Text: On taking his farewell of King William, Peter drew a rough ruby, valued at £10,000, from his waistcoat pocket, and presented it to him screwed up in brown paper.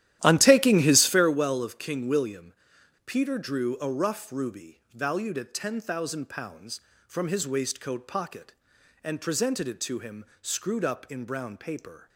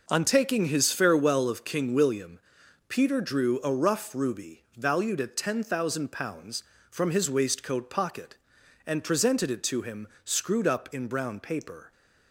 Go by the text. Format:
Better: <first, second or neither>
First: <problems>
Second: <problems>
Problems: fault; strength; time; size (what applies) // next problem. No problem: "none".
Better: second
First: starts louder than the rest; strong; until 1.3 s; 13 dB // pauses between "him" and "screwed"; slight; at 10.2 s; 0.16 s long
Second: pauses between "him" and "screwed"; slight; at 10.0 s; 0.16 s long